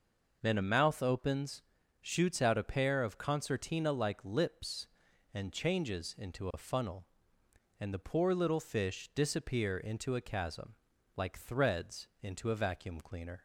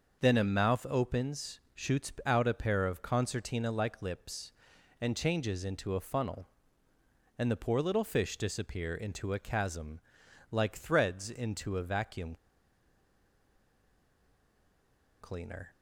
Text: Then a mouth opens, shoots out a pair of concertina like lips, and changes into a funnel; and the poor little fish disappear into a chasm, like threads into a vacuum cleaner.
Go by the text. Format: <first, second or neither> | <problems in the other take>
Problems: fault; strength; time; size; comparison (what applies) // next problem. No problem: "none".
first | starts louder than the rest; noticeable; until 1.2 s; 6 dB // pauses between "vacuum" and "cleaner"; strong; at 12.3 s; 2.8 s long